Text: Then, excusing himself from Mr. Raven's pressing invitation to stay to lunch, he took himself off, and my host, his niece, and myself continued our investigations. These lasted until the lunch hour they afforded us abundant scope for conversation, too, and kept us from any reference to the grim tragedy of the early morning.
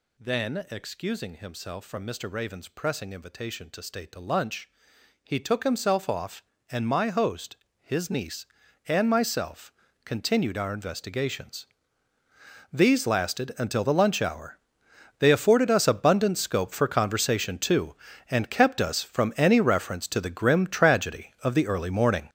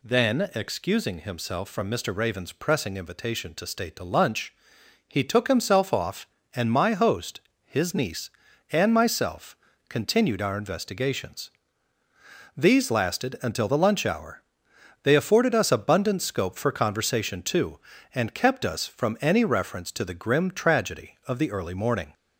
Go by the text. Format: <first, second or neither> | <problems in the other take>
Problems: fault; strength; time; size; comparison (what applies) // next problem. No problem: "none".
second | gets louder; strong; throughout; 10 dB // pauses between "myself" and "continued"; slight; at 9.7 s; 0.32 s long; slight in the second // pauses between "hour" and "they"; noticeable; at 14.5 s; 0.62 s long; noticeable in the second